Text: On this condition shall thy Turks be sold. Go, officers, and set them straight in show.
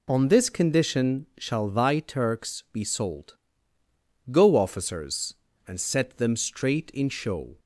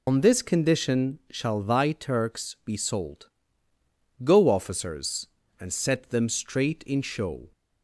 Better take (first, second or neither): first